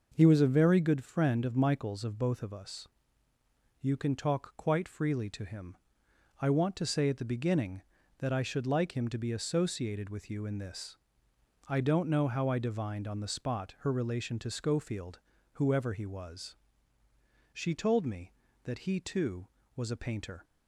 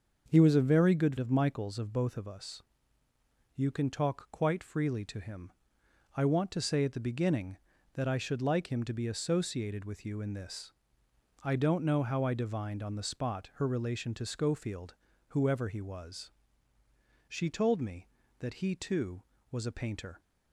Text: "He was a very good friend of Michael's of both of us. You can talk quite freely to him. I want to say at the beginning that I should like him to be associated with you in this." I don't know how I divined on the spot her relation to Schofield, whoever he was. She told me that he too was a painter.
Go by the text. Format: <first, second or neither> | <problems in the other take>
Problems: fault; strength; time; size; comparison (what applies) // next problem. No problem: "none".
first | starts louder than the rest; noticeable; until 1.3 s; 6 dB // skips "friend"; at 1.1 s